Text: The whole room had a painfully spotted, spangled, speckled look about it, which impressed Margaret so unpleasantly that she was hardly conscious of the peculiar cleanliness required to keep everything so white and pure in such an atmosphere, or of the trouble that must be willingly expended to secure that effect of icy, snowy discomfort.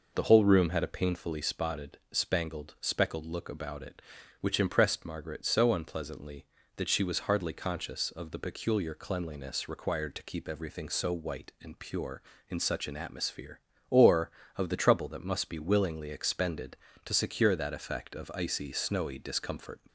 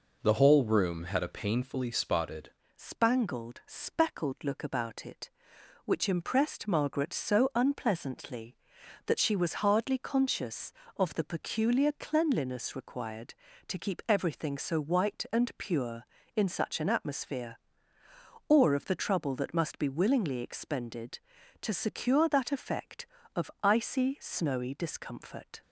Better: first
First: none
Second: changes voice at "spangled"; from 2.7 s on; 22.9 s long

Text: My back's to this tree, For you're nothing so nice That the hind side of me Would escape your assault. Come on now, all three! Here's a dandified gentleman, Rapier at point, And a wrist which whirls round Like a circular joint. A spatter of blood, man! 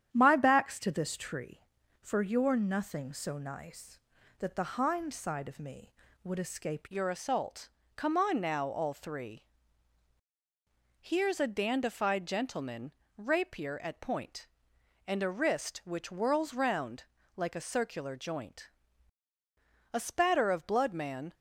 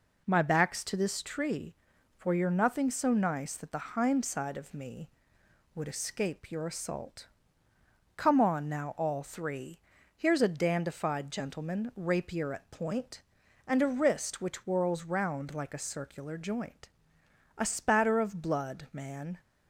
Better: second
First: starts louder than the rest; strong; until 1.1 s; 9.5 dB // changes voice at "your"; from 6.8 s on; 14.5 s long // pauses between "round" and "Like"; slight; at 17.0 s; 0.32 s long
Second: none

